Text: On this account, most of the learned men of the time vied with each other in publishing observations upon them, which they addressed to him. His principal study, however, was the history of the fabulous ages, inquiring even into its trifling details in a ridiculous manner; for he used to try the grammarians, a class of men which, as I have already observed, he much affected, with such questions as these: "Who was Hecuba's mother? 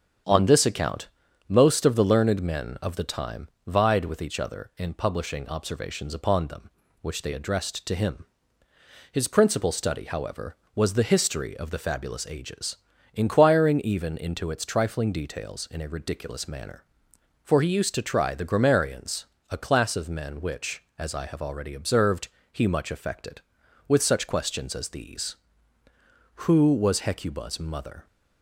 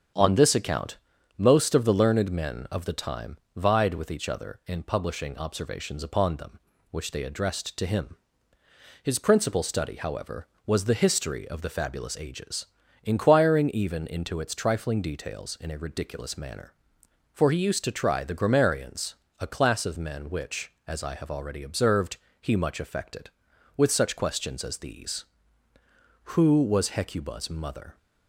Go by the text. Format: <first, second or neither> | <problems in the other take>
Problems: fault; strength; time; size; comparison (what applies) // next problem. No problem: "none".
neither | starts louder than the rest; strong; the same in both // pauses between "time" and "vied"; slight; the same in both